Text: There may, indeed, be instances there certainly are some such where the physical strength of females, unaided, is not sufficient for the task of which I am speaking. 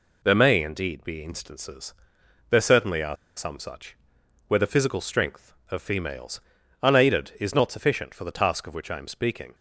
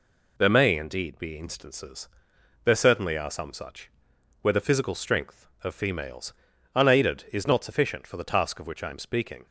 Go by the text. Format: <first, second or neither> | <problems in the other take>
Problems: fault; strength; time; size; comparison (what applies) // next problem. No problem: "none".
second | pauses between "instances" and "there"; noticeable; at 1.9 s; 0.56 s long; noticeable in the second // pauses between "are" and "some"; slight; at 3.1 s; 0.20 s long // pauses between "such" and "where"; noticeable; at 3.9 s; 0.50 s long; noticeable in the second